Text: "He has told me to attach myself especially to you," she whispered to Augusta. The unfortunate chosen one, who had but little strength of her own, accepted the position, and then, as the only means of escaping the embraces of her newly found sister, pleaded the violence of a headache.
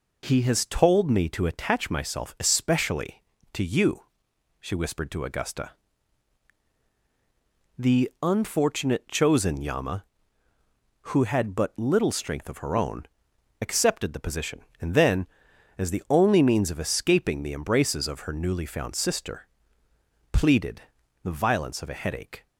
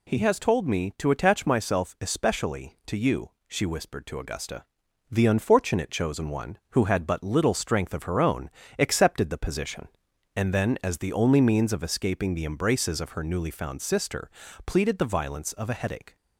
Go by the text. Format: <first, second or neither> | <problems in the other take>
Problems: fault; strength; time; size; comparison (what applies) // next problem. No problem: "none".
second | says "yama" for "one"; at 9.6 s // pauses between "pleaded" and "the"; at 20.8 s; 0.42 s long